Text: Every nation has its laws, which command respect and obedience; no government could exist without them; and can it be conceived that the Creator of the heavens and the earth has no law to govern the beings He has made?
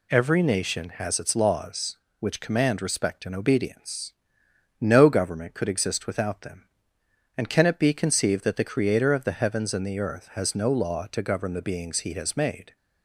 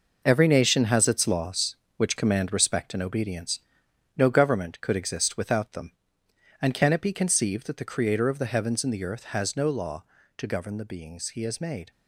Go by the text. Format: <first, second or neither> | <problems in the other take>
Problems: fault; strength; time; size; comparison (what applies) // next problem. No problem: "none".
first | gets quieter; strong; throughout; 9.5 dB